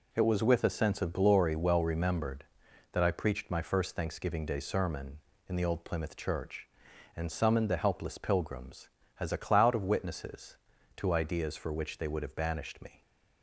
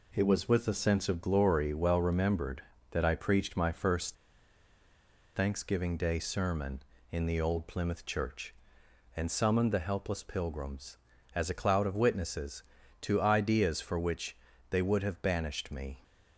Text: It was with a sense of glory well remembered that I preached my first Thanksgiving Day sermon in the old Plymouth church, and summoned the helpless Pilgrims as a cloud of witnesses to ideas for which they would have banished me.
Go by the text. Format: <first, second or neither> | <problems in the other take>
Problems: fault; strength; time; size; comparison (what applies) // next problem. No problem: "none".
first | pauses between "first" and "Thanksgiving"; at 4.1 s; 1.2 s long // pauses between "which" and "they"; slight; at 14.3 s; 0.34 s long